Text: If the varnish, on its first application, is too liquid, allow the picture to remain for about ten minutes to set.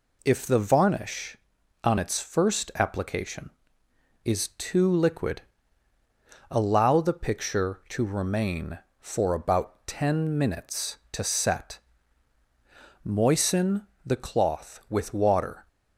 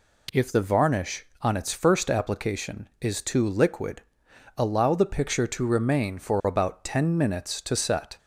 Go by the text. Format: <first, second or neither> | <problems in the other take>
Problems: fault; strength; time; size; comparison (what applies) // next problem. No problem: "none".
second | goes on to say "Moisten the cloth with water"; strong; from 13.0 s on; 2.6 s long